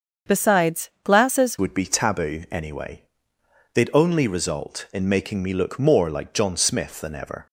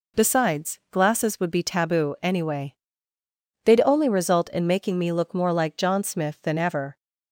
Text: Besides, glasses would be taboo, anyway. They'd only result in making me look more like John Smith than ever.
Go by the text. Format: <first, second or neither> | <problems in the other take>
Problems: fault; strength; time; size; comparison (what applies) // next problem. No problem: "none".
second | starts louder than the rest; until 1.4 s; 7 dB // changes voice at "would"; from 1.5 s on; 5.9 s long